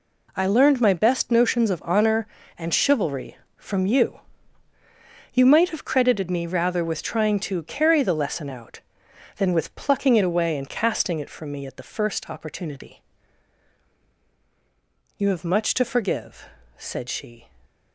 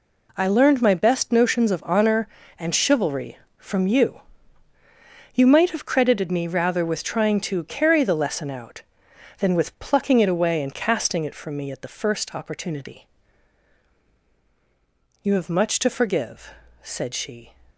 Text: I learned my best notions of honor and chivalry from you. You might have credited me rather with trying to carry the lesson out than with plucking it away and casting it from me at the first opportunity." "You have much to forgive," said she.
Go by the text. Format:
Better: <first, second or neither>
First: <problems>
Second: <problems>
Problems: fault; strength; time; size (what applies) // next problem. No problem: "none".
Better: neither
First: none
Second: none